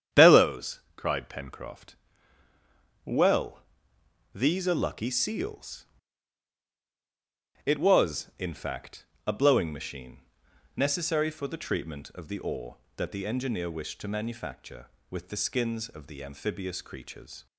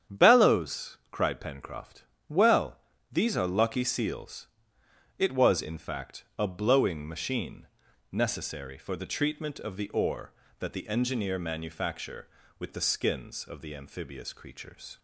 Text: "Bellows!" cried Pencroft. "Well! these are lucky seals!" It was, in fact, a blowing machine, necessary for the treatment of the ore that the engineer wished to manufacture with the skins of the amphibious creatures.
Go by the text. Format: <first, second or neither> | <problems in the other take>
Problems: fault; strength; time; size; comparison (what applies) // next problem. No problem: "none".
first | starts louder than the rest; strong; until 1.2 s; 8.5 dB; strong in the first // skips "wished to"; at 11.3 s